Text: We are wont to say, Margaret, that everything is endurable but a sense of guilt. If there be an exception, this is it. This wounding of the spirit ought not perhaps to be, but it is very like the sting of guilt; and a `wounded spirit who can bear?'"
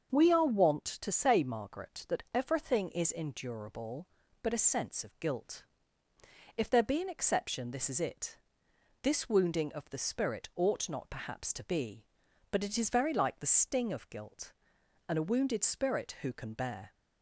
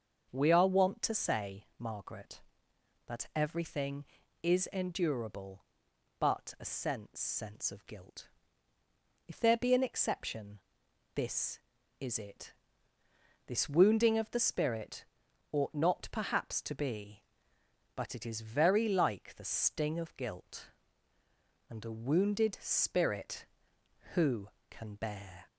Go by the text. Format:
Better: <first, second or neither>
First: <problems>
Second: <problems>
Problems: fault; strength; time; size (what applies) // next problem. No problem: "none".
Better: first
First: starts louder than the rest; until 1.1 s; 6.5 dB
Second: starts louder than the rest; until 1.3 s; 6.5 dB // says "sense" twice; at 7.2 s // pauses between "spirit" and "ought"; noticeable; at 15.0 s; 0.46 s long